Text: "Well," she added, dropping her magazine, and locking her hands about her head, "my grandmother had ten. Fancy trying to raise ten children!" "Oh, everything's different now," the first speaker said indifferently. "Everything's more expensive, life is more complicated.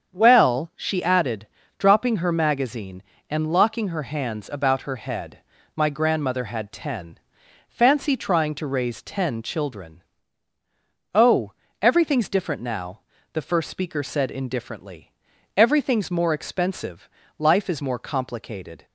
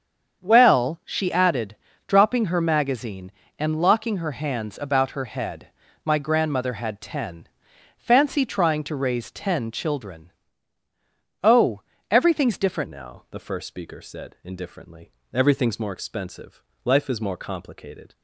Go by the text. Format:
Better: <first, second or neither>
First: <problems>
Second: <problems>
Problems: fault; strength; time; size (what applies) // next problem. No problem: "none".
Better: first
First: starts louder than the rest; until 1.1 s; 7 dB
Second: starts louder than the rest; until 1.4 s; 7 dB // changes voice at "now"; from 12.8 s on; 5.3 s long